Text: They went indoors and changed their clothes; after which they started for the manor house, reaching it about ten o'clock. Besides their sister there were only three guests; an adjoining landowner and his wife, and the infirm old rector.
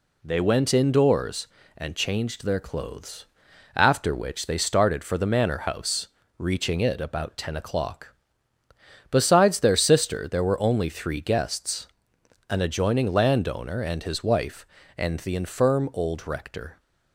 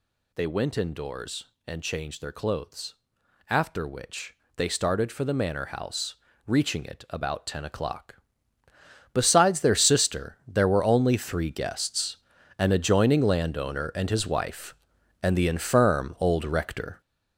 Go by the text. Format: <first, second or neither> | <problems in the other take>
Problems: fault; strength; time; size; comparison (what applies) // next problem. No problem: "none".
first | gets louder; strong; throughout; 7.5 dB // pauses between "which" and "they"; slight; at 4.3 s; 0.20 s long